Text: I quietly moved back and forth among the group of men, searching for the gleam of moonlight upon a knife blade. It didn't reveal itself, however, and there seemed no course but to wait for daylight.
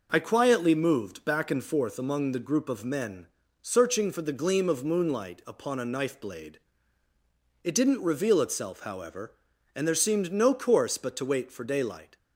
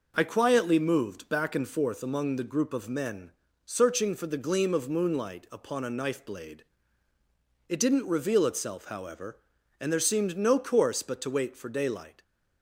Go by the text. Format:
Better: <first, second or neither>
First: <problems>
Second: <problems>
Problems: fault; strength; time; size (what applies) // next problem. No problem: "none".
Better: neither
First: none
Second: none